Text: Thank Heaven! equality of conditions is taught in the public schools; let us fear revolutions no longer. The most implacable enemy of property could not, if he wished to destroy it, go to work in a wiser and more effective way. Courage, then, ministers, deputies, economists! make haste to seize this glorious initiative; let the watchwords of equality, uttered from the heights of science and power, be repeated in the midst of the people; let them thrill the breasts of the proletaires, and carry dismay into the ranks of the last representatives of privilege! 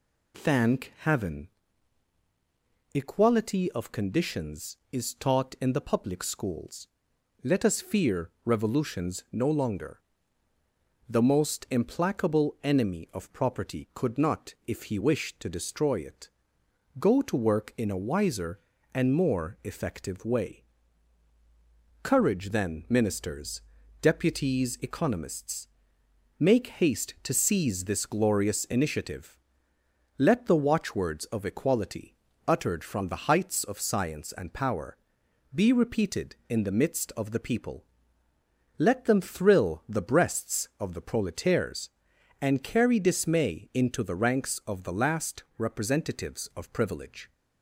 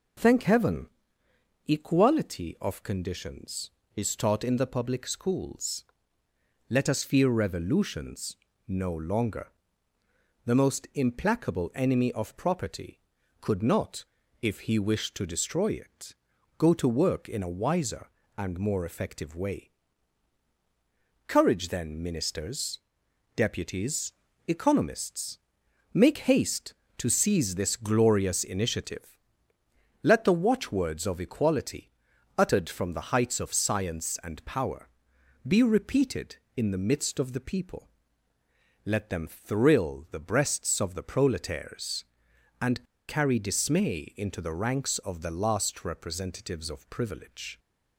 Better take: first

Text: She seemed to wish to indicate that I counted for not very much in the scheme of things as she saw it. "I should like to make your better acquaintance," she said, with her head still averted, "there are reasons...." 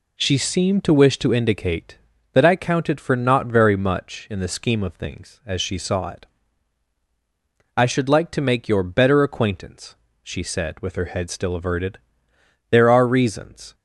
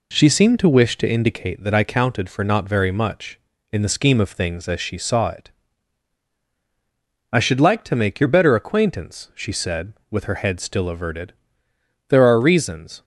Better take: neither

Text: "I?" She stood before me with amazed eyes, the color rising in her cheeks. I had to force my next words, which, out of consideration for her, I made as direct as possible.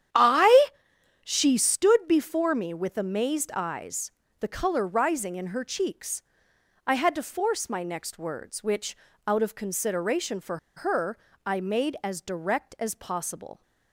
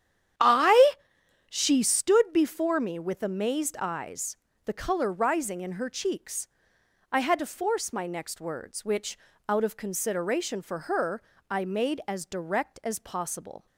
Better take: second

